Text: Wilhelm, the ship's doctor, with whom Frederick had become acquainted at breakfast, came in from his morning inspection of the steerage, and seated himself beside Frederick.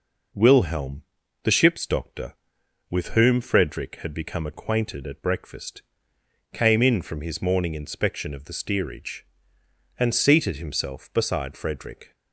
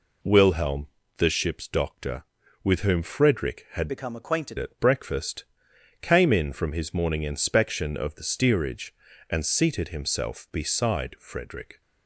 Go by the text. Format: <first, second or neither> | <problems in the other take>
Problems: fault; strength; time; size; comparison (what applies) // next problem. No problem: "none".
first | changes voice from "become" to "acquainted"; from 3.8 to 4.5 s; 0.7 s long